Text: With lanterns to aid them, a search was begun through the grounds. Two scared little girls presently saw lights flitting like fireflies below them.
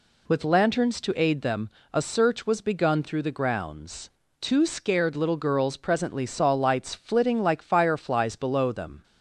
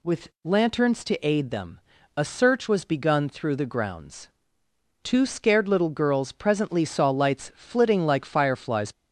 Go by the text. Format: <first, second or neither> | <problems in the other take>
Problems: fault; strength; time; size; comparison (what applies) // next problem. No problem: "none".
first | stops before "below them"; at 8.9 s